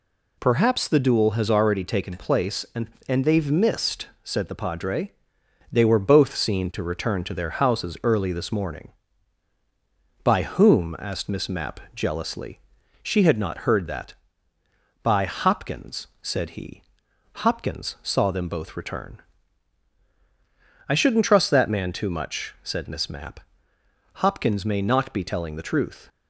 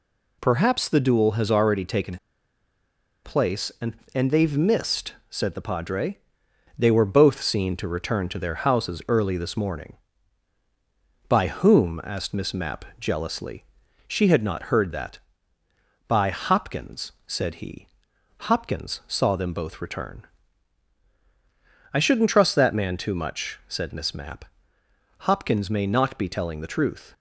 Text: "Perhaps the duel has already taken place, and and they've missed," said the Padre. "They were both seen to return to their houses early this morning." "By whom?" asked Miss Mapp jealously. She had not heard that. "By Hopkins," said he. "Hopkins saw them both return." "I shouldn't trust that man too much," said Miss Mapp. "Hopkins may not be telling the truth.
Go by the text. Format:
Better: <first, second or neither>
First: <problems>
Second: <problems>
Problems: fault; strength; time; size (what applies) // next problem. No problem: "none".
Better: first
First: none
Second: pauses between "taken" and "place"; at 2.1 s; 1.0 s long